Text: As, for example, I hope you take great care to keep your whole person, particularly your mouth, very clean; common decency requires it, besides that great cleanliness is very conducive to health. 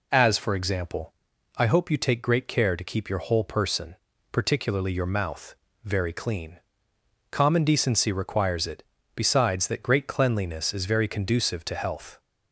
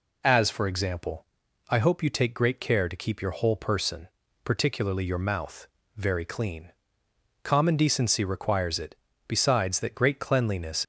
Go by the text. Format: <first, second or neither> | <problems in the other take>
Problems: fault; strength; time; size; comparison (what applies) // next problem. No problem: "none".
first | stops before "is very conducive to health"; at 10.8 s